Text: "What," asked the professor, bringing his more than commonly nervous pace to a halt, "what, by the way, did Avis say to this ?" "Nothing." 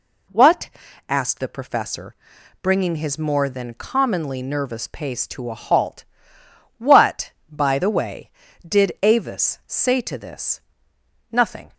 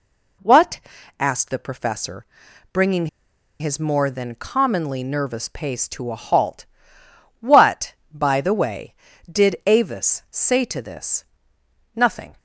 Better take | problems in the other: first | pauses between "bringing" and "his"; noticeable; at 3.0 s; 0.53 s long

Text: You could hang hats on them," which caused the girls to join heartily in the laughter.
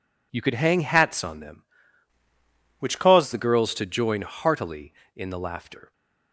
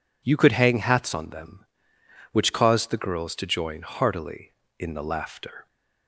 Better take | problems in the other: second | changes voice from "which" to "caused"; from 2.7 to 3.3 s; 0.6 s long

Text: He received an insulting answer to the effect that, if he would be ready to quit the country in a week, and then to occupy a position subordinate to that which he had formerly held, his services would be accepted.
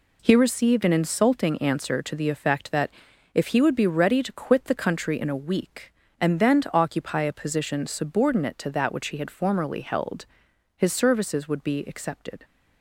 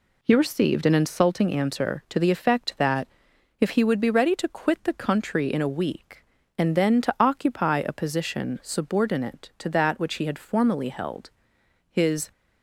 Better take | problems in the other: first | stops before "services would be accepted"; at 12.3 s

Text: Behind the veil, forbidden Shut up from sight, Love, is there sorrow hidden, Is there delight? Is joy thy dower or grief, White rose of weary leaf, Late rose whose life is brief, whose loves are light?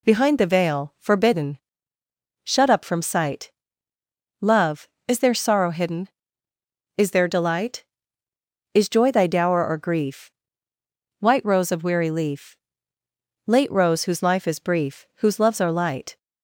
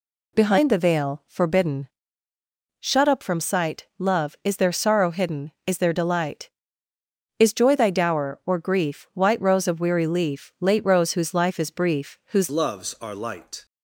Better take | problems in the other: first | pauses between "forbidden" and "Shut"; noticeable; at 1.8 s; 0.94 s long; noticeable in the first // changes voice at "loves"; from 12.4 s on; 1.2 s long

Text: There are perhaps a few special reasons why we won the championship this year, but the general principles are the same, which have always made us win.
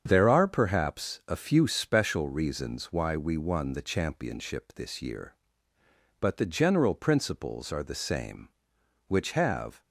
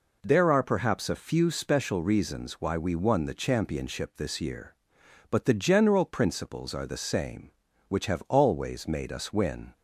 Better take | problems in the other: second | starts louder than the rest; strong; until 1.0 s; 7.5 dB // stops before "always made us win"; at 9.8 s

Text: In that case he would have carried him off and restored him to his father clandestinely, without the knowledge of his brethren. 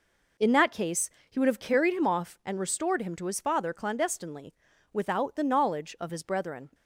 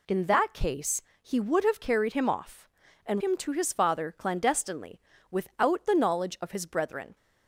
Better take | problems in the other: first | pauses between "case" and "he"; slight; at 1.0 s; 0.22 s long; slight in the first // skips "restored"; at 3.2 s

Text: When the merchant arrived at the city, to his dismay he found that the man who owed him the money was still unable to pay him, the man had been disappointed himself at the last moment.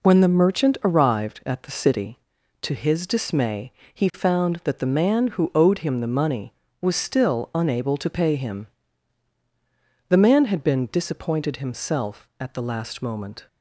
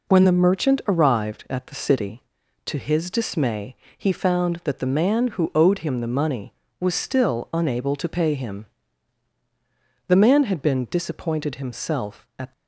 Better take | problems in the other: first | pauses between "dismay" and "he"; slight; at 3.7 s; 0.22 s long; slight in the first // stops before "the last moment"; at 12.5 s

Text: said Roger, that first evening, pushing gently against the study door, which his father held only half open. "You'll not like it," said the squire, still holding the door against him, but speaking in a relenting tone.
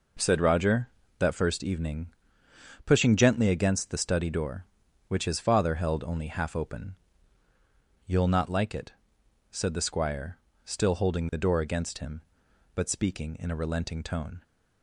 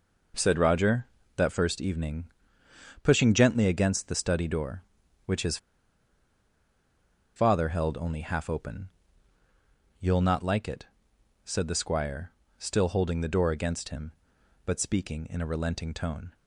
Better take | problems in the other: first | pauses between "his" and "father"; strong; at 5.5 s; 1.7 s long

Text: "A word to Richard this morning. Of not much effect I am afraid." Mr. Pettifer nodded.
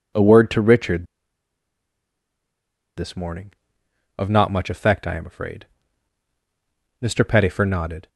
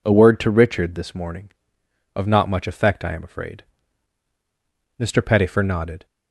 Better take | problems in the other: second | pauses between "Richard" and "this"; strong; at 1.0 s; 1.9 s long

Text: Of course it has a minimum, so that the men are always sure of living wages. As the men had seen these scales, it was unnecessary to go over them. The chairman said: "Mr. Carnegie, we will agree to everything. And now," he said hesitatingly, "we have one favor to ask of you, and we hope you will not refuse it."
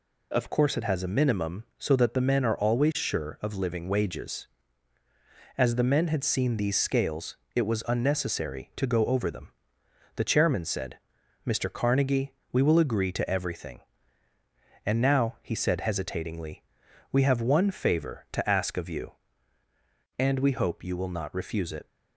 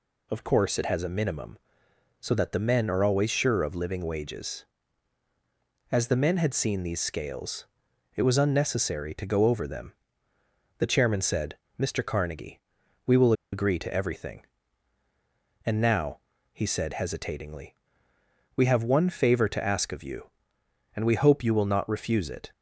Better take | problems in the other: first | pauses between "will" and "agree"; slight; at 13.3 s; 0.20 s long

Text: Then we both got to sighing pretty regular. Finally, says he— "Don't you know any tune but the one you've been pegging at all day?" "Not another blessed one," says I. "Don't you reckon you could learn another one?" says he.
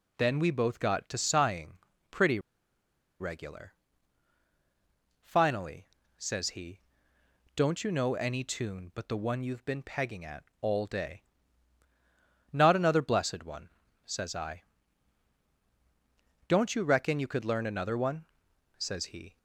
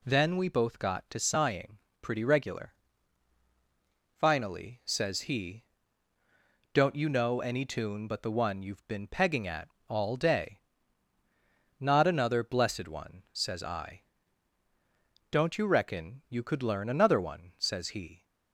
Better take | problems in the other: second | pauses between "sighing" and "pretty"; slight; at 1.7 s; 0.32 s long; slight in the second // pauses between "pretty" and "regular"; noticeable; at 2.3 s; 0.81 s long // pauses between "at" and "all"; slight; at 10.4 s; 0.16 s long; slight in the second

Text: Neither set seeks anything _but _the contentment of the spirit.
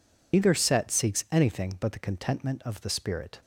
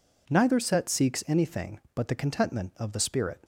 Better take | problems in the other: second | loses the start of "Neither"; at 0.3 s; 115 ms

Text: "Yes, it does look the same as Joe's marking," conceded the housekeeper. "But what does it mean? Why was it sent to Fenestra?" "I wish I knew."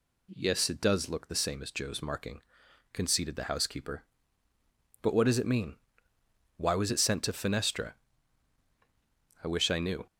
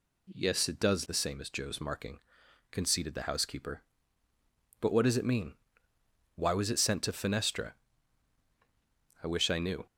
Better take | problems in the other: first | skips "look"; at 1.0 s

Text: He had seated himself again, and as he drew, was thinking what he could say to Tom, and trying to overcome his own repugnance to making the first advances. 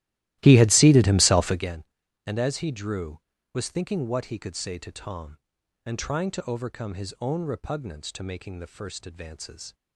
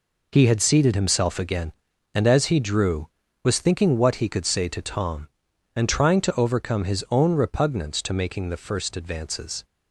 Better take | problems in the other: second | starts louder than the rest; strong; until 1.8 s; 15.5 dB

